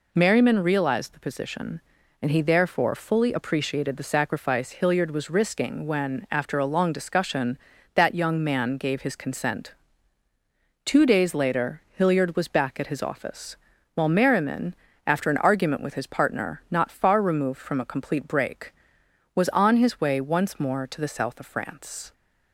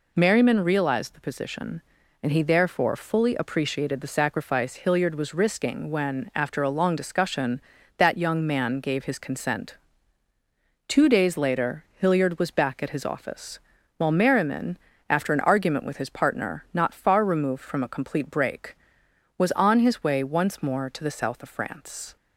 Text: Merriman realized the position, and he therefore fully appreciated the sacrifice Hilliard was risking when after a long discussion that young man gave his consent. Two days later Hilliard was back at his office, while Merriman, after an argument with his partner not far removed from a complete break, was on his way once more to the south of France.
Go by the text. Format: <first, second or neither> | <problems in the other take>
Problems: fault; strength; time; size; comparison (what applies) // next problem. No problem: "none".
neither | pauses between "later" and "Hilliard"; slight; the same in both